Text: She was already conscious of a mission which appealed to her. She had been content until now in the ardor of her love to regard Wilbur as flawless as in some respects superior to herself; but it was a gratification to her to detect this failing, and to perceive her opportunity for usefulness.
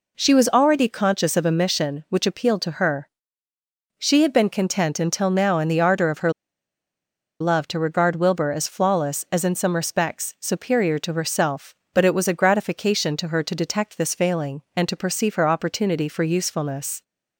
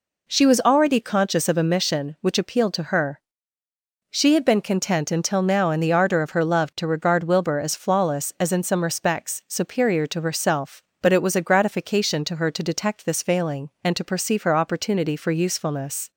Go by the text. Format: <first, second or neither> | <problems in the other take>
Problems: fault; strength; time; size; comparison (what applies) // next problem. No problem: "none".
second | pauses between "her" and "love"; at 6.3 s; 1.0 s long